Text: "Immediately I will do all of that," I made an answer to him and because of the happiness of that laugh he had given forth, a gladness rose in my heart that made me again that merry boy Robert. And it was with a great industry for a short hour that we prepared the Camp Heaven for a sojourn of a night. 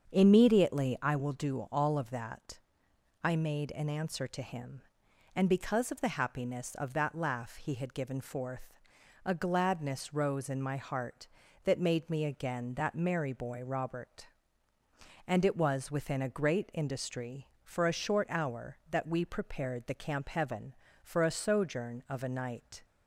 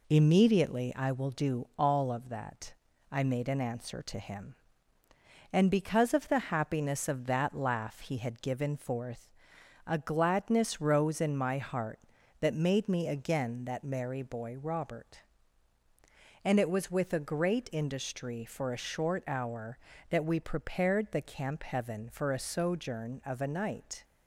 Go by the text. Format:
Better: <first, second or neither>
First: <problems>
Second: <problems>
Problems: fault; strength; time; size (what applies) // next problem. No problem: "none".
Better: second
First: starts louder than the rest; strong; until 1.1 s; 7 dB // says "within" for "with"; at 15.9 s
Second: none